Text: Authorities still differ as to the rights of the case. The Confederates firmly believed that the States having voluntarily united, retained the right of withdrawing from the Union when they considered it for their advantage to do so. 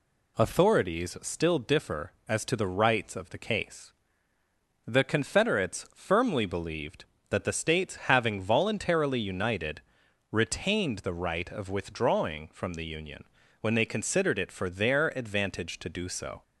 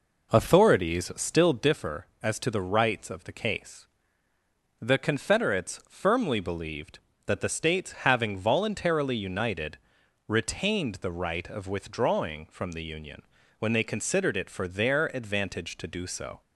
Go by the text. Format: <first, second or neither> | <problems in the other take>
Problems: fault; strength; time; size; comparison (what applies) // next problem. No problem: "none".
first | starts louder than the rest; noticeable; until 1.8 s; 4.5 dB // pauses between "Union" and "when"; slight; at 13.2 s; 0.36 s long; slight in the first